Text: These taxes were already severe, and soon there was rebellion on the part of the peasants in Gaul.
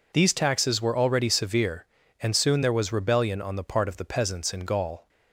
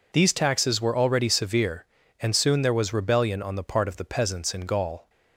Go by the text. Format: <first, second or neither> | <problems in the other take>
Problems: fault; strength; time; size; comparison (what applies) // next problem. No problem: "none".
neither | none